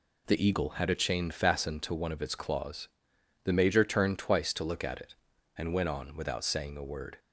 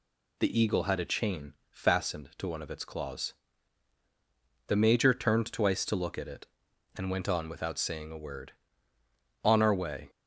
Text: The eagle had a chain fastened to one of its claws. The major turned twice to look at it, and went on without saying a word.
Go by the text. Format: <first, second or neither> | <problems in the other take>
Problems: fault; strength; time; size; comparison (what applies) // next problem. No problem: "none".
first | pauses between "chain" and "fastened"; slight; at 1.5 s; 0.16 s long // goes on to say "On our way"; noticeable; from 9.4 s on; 0.66 s long